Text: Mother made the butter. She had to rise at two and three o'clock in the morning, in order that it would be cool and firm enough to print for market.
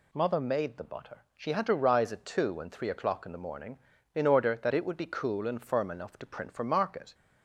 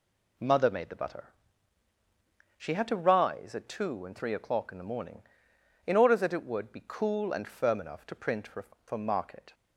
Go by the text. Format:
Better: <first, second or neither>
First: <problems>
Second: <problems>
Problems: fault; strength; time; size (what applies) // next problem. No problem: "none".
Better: first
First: none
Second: says "for" twice; at 8.8 s